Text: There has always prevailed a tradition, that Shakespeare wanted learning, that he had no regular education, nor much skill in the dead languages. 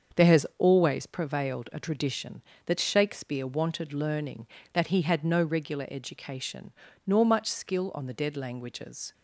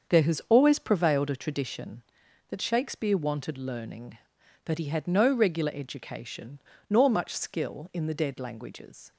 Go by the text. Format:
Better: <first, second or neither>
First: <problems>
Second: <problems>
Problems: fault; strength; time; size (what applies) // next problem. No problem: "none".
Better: second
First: starts louder than the rest; until 1.2 s; 6.5 dB // says "on" for "in"; at 7.9 s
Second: starts louder than the rest; until 1.1 s; 7 dB